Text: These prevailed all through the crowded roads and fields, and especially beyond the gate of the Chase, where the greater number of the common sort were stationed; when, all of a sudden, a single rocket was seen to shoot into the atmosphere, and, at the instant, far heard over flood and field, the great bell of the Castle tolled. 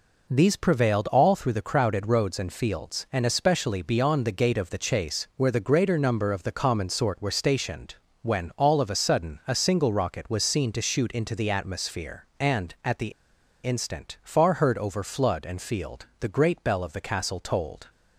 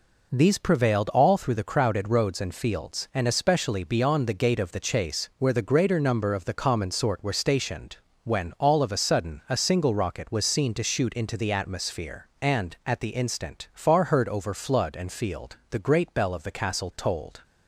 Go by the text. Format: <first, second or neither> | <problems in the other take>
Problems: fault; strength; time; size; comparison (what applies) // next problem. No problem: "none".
second | pauses between "the" and "instant"; noticeable; at 13.1 s; 0.53 s long